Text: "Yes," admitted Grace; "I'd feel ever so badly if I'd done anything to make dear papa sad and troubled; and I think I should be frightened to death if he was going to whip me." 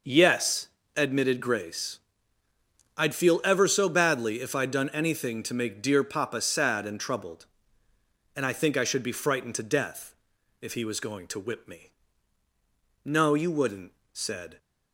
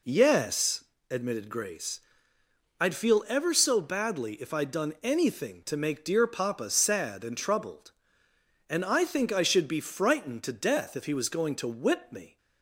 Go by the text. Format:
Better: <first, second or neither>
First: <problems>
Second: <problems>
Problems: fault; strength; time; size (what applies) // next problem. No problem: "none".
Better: second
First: pauses between "death" and "if"; noticeable; at 10.1 s; 0.46 s long // goes on to say "No you wouldn't said"; from 13.0 s on; 1.5 s long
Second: none